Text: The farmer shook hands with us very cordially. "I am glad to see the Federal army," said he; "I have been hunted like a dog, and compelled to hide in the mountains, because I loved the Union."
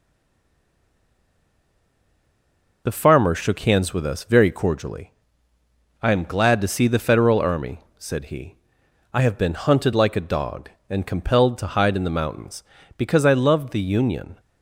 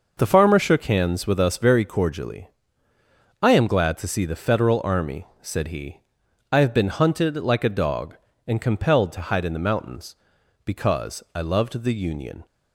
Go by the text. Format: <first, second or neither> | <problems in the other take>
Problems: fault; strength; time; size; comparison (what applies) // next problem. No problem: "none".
second | stays silent before the first word; strong; until 2.8 s; 2.8 s long